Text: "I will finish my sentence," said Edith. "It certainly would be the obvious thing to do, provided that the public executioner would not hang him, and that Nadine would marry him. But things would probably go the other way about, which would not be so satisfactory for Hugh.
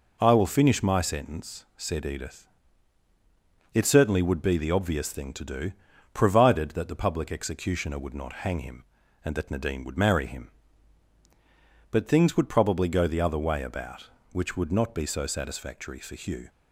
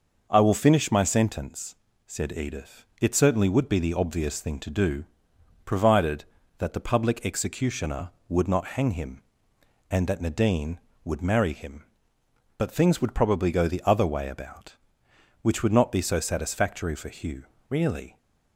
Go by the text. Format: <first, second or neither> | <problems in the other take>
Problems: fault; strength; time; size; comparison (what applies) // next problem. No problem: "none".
first | goes on to say "Really"; slight; from 17.6 s on; 0.48 s long